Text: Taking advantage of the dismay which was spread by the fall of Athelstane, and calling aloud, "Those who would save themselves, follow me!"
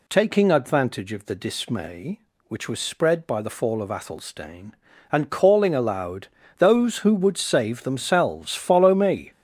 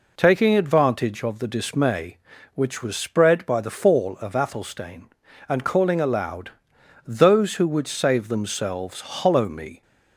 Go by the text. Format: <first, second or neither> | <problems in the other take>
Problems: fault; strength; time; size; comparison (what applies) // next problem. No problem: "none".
first | says "hollow" for "follow"; at 9.0 s